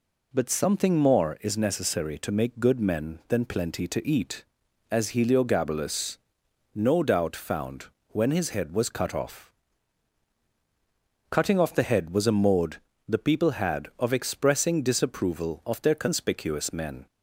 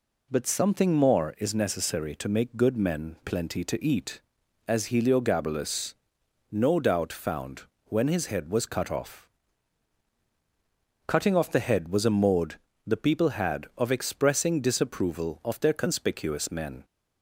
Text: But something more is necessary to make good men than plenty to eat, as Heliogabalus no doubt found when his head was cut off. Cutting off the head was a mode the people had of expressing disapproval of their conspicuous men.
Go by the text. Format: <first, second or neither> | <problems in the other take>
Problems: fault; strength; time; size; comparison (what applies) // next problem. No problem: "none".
first | skips "than"; at 3.2 s // pauses between "Heliogabalus" and "no"; noticeable; at 5.9 s; 0.60 s long; noticeable in the first // pauses between "found" and "when"; slight; at 7.6 s; 0.22 s long; slight in the first // pauses between "mode" and "the"; slight; at 12.5 s; 0.26 s long; slight in the first